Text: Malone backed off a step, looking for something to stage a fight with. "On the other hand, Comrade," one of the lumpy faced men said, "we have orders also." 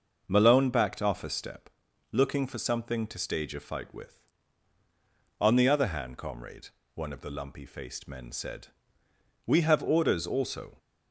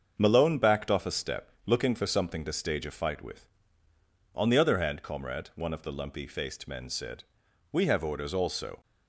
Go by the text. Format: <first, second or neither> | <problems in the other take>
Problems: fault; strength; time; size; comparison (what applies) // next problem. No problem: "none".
neither | starts louder than the rest; the same in both